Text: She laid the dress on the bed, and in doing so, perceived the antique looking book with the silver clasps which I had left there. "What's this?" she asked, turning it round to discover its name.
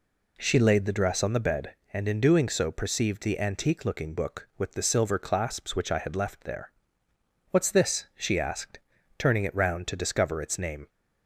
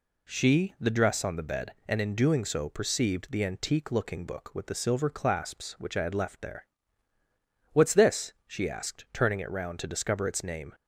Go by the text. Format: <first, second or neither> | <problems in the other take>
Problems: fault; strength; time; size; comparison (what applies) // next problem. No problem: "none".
first | skips "laid"; at 0.7 s